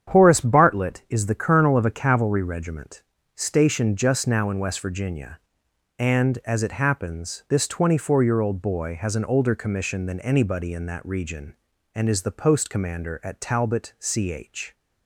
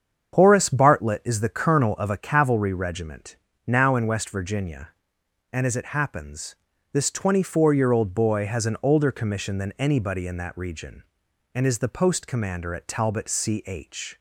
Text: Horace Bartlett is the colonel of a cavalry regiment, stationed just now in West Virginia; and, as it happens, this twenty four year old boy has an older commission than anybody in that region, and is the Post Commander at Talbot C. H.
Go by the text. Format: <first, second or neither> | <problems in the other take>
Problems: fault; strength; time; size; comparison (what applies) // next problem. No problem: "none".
first | starts louder than the rest; strong; until 1.3 s; 7.5 dB; strong in the first // skips "stationed just"; at 3.5 s